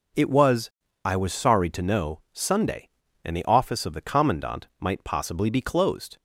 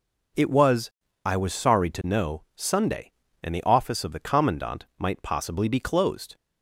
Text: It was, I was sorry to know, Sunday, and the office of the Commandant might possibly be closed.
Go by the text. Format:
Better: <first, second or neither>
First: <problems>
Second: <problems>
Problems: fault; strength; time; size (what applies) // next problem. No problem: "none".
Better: neither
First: none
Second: none